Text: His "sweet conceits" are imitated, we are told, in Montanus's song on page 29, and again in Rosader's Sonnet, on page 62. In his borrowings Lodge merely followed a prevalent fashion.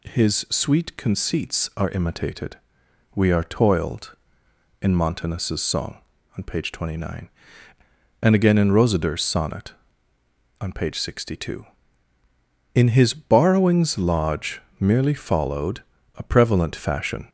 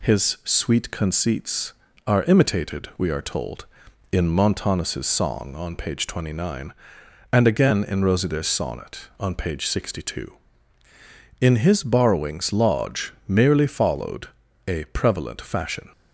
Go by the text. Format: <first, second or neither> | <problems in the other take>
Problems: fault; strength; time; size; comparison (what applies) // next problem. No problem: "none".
second | says "toiled" for "told"; at 3.4 s // pauses between "Lodge" and "merely"; slight; at 14.6 s; 0.18 s long // pauses between "followed" and "a"; slight; at 15.8 s; 0.34 s long; slight in the second